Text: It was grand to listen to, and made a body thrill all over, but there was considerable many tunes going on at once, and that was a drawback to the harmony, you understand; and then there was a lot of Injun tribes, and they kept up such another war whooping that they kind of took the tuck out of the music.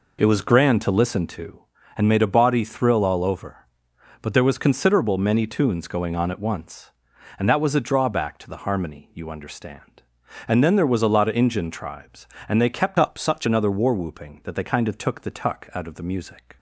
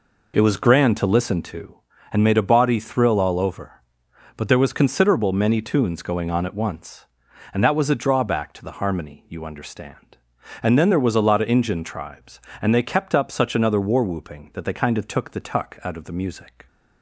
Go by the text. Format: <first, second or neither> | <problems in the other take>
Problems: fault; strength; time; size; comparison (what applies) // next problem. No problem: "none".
second | changes voice from "up" to "such"; from 12.9 to 13.4 s; 0.5 s long